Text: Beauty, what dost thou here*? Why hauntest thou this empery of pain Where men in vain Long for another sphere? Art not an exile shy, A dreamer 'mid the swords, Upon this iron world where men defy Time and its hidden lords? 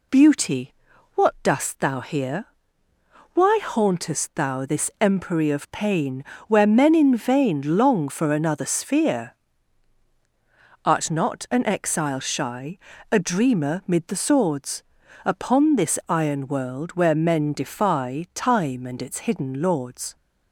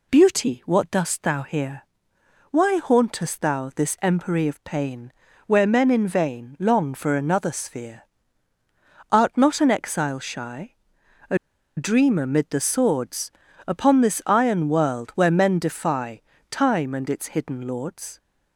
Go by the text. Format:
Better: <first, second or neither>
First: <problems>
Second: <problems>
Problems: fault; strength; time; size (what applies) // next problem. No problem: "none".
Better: first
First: pauses between "pain" and "Where"; slight; at 6.2 s; 0.22 s long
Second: pauses between "pain" and "Where"; slight; at 5.1 s; 0.34 s long // pauses between "A" and "dreamer"; at 11.3 s; 0.39 s long // pauses between "defy" and "Time"; slight; at 16.2 s; 0.26 s long